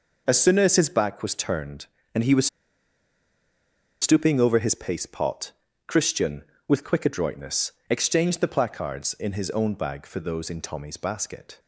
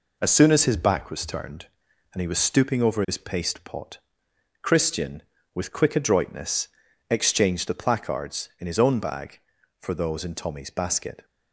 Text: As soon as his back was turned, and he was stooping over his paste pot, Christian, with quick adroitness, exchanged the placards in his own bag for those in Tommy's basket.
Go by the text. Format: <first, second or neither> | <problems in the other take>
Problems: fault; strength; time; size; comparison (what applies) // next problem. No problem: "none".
second | pauses between "was" and "stooping"; strong; at 2.4 s; 1.5 s long